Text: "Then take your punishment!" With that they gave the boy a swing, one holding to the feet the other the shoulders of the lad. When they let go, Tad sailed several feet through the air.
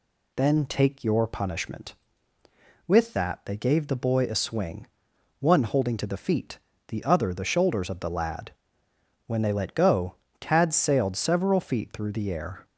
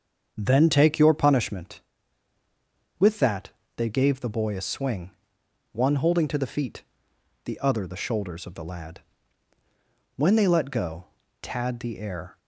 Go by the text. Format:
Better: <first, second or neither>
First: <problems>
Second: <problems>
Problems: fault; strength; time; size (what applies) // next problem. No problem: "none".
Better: first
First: pauses between "feet" and "the"; slight; at 6.5 s; 0.32 s long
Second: starts louder than the rest; strong; until 1.3 s; 7 dB // pauses between "that" and "they"; slight; at 3.4 s; 0.26 s long // pauses between "feet" and "the"; noticeable; at 6.8 s; 0.62 s long // skips "sailed several feet through"; at 11.7 s